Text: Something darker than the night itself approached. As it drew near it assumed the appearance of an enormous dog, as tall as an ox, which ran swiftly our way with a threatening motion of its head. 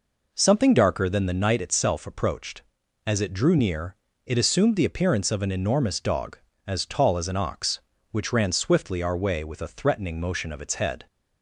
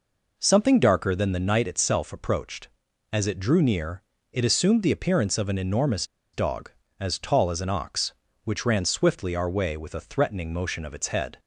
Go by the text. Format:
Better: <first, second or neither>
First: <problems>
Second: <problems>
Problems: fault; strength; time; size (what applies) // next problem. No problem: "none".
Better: first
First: pauses between "near" and "it"; slight; at 3.9 s; 0.30 s long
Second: pauses between "near" and "it"; slight; at 4.0 s; 0.30 s long // pauses between "enormous" and "dog"; slight; at 6.0 s; 0.28 s long